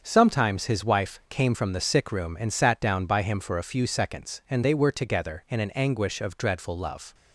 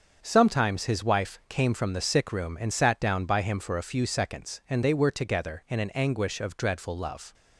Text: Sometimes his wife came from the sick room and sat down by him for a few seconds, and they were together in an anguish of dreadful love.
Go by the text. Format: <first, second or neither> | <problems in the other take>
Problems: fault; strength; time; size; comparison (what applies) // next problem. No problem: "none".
neither | starts louder than the rest; strong; the same in both